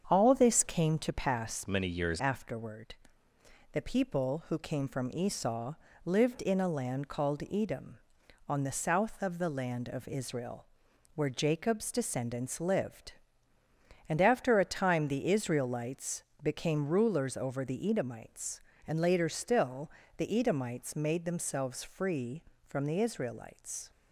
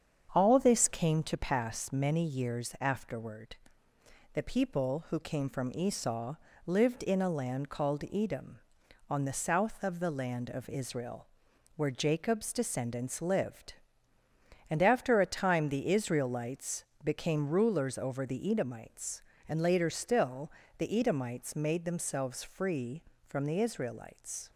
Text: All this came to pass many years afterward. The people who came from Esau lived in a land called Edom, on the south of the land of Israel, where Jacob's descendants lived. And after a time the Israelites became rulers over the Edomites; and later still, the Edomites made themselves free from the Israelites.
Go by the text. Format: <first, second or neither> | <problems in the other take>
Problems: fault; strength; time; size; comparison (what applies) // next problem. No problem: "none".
second | starts louder than the rest; strong; until 1.0 s; 7.5 dB; strong in the second // changes voice from "many" to "years"; from 1.6 to 2.1 s; 0.5 s long // pauses between "Esau" and "lived"; slight; at 5.7 s; 0.32 s long; slight in the second // pauses between "Israelites" and "became"; slight; at 16.2 s; 0.18 s long; slight in the second